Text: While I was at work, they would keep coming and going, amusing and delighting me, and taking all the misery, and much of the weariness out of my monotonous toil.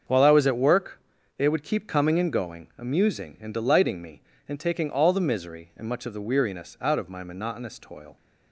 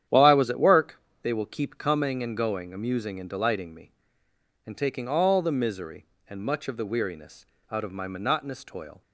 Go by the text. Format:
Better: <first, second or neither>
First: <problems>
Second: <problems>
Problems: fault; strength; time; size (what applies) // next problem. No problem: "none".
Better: first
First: starts louder than the rest; until 1.4 s; 6.5 dB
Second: starts louder than the rest; strong; until 1.3 s; 10 dB // says "will" for "would"; at 1.3 s // pauses between "weariness" and "out"; slight; at 7.4 s; 0.26 s long